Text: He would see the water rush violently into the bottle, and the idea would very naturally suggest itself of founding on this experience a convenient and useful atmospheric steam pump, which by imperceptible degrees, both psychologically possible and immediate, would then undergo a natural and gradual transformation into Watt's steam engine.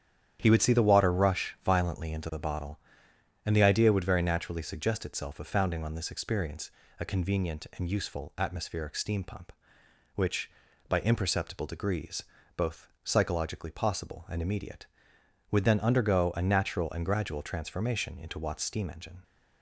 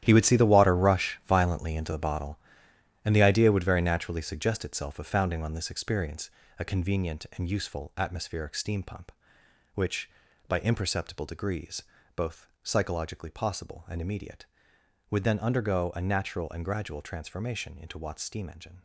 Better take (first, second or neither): first